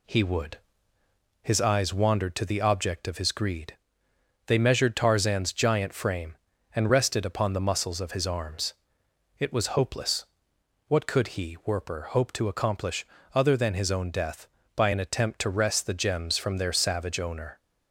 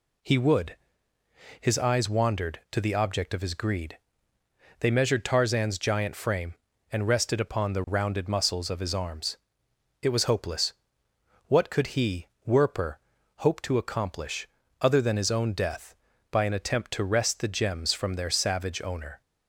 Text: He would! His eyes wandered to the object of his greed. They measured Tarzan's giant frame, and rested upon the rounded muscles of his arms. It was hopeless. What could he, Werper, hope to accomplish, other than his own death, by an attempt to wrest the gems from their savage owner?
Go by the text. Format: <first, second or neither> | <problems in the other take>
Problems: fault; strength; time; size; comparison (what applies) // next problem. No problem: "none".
second | skips "rounded"; at 7.6 s